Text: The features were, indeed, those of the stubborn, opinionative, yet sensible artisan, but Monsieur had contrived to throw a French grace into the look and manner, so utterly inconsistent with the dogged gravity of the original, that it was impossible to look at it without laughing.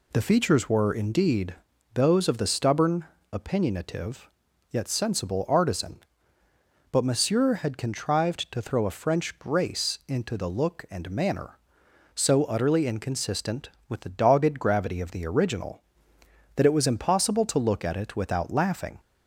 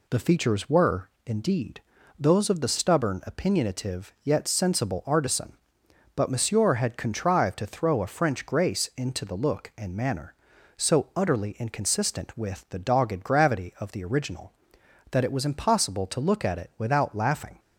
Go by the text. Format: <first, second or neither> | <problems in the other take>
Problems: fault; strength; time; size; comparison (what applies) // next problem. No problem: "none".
neither | none